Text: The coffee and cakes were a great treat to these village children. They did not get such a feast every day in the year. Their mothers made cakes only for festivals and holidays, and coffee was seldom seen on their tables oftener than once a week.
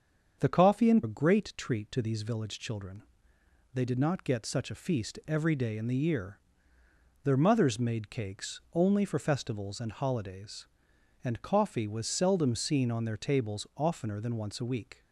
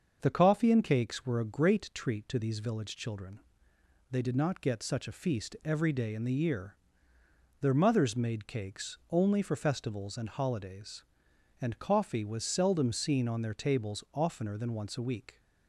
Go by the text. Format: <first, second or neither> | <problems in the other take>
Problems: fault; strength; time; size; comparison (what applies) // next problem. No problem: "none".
second | starts louder than the rest; until 1.4 s; 7 dB; also in the second // skips "cakes were"; at 1.0 s